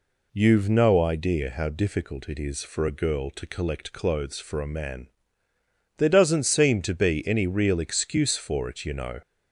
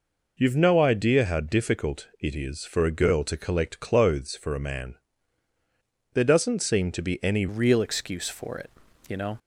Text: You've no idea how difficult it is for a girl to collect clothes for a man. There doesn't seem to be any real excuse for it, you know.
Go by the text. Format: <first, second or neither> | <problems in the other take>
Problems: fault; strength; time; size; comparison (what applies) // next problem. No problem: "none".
first | changes voice at "real"; from 7.4 s on; 1.9 s long